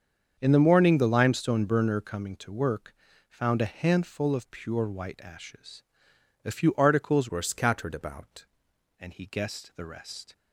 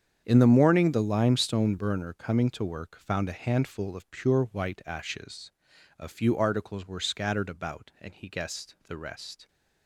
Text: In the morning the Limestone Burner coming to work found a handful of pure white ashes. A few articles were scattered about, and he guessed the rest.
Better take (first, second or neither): second